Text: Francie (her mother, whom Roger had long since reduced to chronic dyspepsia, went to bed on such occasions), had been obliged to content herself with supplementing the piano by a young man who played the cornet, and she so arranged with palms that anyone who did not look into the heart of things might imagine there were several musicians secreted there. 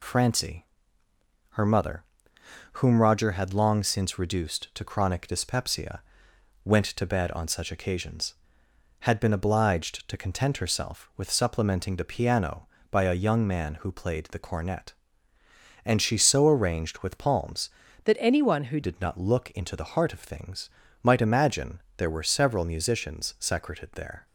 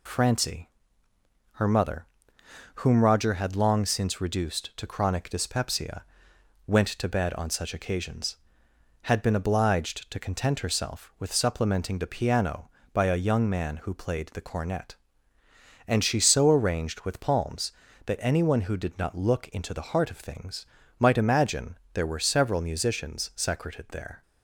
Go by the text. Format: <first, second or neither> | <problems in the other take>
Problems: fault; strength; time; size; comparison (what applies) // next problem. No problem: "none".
second | changes voice from "that" to "who"; from 18.0 to 18.7 s; 0.7 s long // pauses between "things" and "might"; slight; at 20.6 s; 0.34 s long; slight in the second // pauses between "imagine" and "there"; slight; at 21.8 s; 0.16 s long; slight in the second